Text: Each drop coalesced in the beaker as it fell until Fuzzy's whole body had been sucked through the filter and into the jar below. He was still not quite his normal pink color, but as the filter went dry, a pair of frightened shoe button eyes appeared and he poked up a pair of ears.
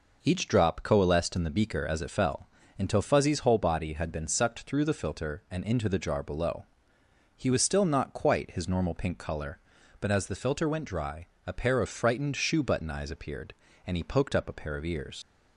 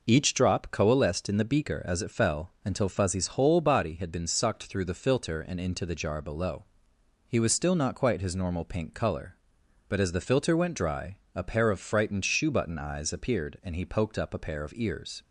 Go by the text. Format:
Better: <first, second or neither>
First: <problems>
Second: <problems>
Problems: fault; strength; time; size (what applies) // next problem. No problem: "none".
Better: second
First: pauses between "fell" and "until"; slight; at 2.4 s; 0.32 s long // leaves "ears" unfinished; at 15.2 s; 70 ms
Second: none